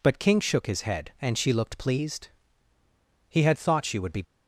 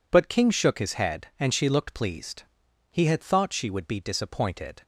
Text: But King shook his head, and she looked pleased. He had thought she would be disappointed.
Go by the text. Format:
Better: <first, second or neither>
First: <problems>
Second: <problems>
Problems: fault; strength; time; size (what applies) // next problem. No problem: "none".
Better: second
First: stops before "disappointed"; at 4.2 s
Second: none